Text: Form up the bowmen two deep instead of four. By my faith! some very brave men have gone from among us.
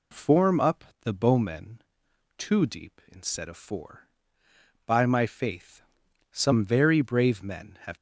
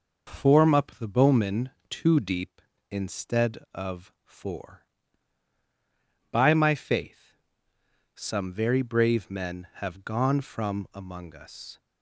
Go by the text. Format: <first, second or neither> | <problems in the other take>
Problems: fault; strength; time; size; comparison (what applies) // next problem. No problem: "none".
second | pauses between "up" and "the"; slight; at 0.8 s; 0.20 s long // pauses between "bowmen" and "two"; noticeable; at 1.8 s; 0.56 s long; slight in the second // stops before "gone from among us"; at 7.9 s